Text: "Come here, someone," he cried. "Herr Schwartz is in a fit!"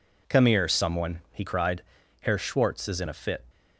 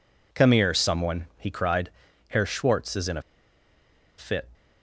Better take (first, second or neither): first